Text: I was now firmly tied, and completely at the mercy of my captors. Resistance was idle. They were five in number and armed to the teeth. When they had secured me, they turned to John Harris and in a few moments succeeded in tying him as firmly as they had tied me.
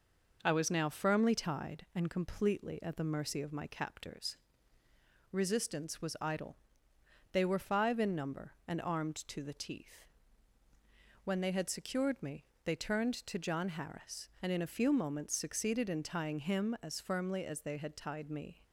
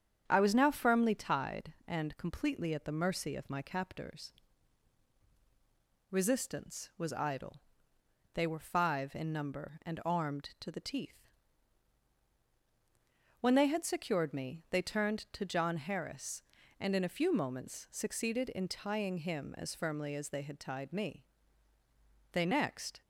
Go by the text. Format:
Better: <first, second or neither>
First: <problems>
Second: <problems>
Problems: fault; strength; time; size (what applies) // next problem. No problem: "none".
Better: first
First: none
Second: starts louder than the rest; strong; until 1.2 s; 8 dB // goes on to say "They next"; noticeable; from 22.3 s on; 0.70 s long